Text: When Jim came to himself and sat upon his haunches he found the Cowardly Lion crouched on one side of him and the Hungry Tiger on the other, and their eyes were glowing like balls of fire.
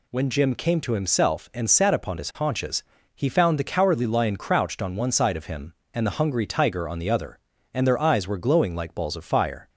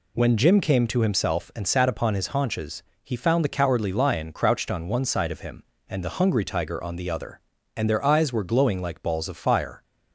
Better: neither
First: pauses between "haunches" and "he"; slight; at 2.8 s; 0.32 s long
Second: pauses between "haunches" and "he"; slight; at 2.8 s; 0.22 s long

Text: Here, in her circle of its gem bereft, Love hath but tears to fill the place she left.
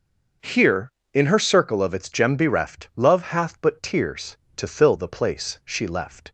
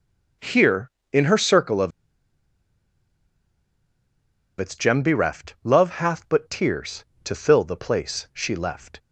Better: first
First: starts louder than the rest; noticeable; until 1.6 s; 6 dB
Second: starts louder than the rest; noticeable; until 1.6 s; 6 dB // pauses between "of" and "its"; strong; at 1.9 s; 2.6 s long

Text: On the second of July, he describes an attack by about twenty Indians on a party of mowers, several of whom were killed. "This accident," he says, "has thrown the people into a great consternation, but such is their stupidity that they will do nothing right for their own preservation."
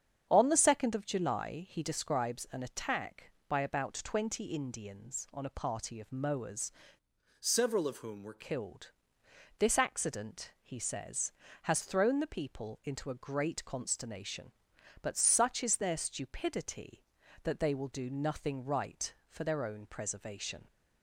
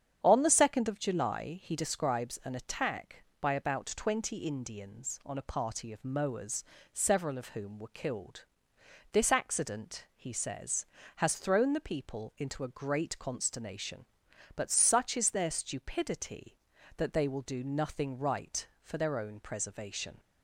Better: second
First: starts louder than the rest; strong; until 1.3 s; 8 dB // changes voice from "several" to "were"; from 7.4 to 8.4 s; 1.0 s long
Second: starts louder than the rest; strong; until 1.2 s; 8.5 dB

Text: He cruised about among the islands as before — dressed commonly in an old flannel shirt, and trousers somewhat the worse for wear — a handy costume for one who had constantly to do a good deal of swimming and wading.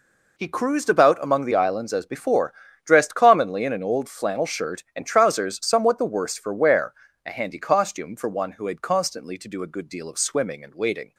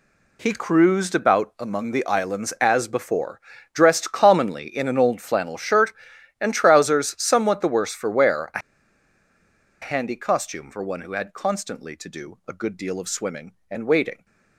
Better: first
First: none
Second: pauses between "a" and "handy"; at 8.5 s; 1.2 s long

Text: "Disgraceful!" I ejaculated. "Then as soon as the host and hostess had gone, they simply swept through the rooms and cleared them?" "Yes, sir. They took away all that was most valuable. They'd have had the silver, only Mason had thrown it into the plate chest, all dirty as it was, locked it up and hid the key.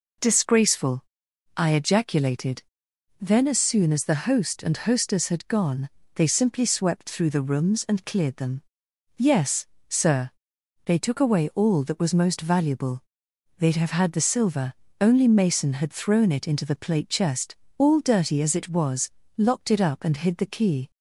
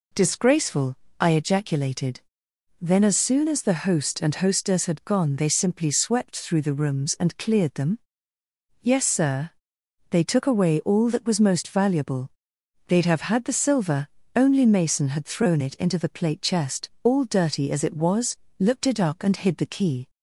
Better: first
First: none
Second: says "looked" for "locked"; at 18.5 s

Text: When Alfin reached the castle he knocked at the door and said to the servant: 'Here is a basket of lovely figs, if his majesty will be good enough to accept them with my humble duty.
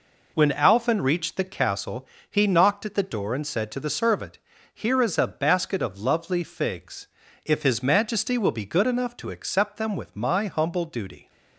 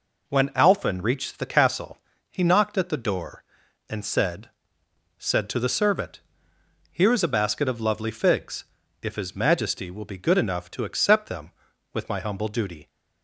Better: first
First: pauses between "castle" and "he"; slight; at 2.0 s; 0.22 s long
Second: pauses between "castle" and "he"; slight; at 1.9 s; 0.34 s long // says "said" twice; at 5.1 s

